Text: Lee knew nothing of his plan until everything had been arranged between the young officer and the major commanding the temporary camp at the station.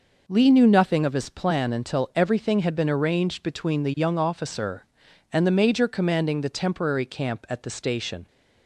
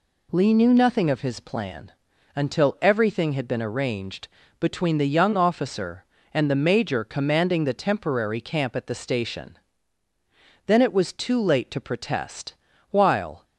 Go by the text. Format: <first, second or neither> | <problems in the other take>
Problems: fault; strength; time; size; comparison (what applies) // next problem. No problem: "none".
first | pauses between "plan" and "until"; at 1.9 s; 0.44 s long // pauses between "arranged" and "between"; slight; at 4.2 s; 0.32 s long // goes on to say "Then it was too late to protest While"; strong; from 10.6 s on; 2.7 s long